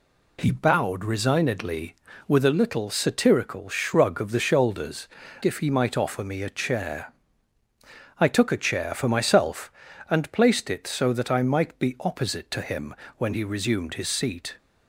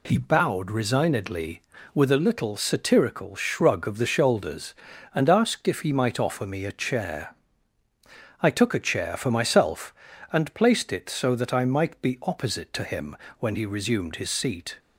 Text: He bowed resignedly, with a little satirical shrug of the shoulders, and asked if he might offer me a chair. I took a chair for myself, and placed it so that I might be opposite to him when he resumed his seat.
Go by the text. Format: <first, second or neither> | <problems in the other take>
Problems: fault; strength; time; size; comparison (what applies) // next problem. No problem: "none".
second | skips "and asked"; at 5.2 s // pauses between "him" and "when"; slight; at 12.9 s; 0.24 s long; slight in the second